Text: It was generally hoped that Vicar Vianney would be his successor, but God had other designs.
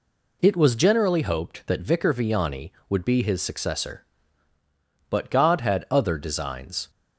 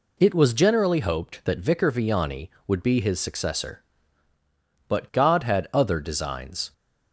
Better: neither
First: none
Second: none

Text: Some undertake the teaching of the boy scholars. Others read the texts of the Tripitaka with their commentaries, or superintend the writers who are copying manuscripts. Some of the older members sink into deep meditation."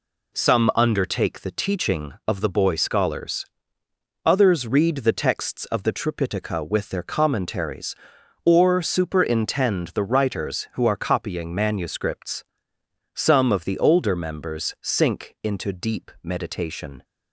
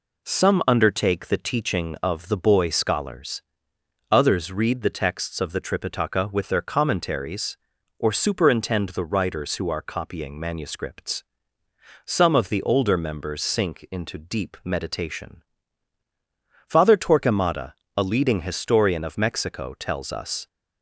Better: first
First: none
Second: goes on to say "Father Torquemada a leading historian of Mexico tells us"; strong; from 16.6 s on; 3.7 s long

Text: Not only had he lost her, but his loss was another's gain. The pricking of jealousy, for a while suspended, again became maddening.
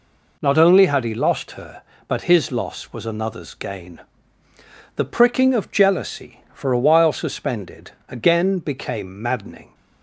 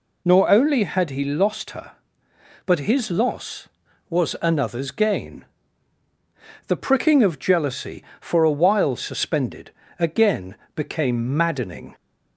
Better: first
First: none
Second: says "Nor" for "Not"; at 0.2 s // pauses between "again" and "became"; slight; at 10.5 s; 0.20 s long

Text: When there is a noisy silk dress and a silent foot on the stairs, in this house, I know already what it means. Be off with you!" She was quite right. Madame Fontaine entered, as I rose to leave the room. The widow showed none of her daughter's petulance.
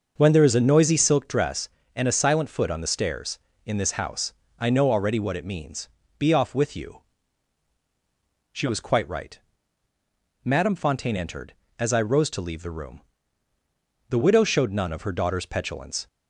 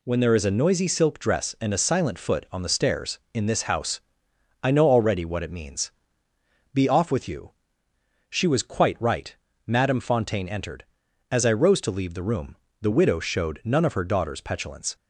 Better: second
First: starts louder than the rest; noticeable; until 1.3 s; 6 dB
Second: none

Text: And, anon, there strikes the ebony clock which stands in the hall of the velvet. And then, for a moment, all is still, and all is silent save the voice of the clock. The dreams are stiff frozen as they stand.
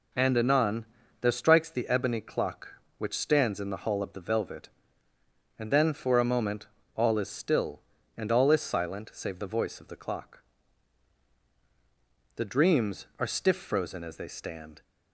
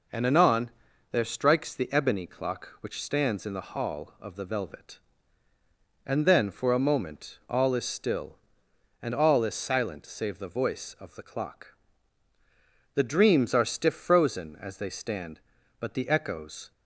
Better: first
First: none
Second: goes on to say "But the echoes"; noticeable; from 15.8 s on; 0.90 s long

